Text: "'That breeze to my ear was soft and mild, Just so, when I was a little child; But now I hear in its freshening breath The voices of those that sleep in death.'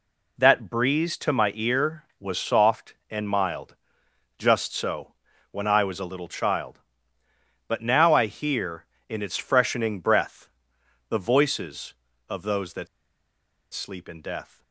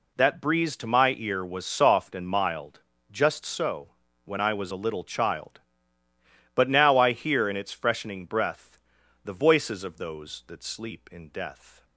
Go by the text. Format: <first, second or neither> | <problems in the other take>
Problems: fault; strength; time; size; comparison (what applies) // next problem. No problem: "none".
second | pauses between "breath" and "The"; noticeable; at 10.4 s; 0.58 s long; noticeable in the second // pauses between "that" and "sleep"; noticeable; at 12.8 s; 0.86 s long